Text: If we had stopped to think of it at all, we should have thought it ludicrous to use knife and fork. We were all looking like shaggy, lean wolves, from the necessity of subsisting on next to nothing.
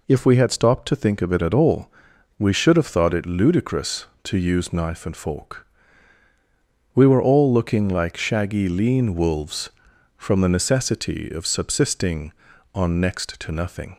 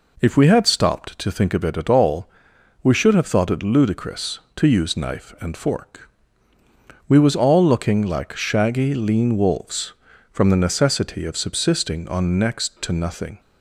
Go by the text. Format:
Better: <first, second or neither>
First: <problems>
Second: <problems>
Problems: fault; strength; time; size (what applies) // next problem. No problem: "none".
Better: first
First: none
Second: says "was" for "were"; at 7.1 s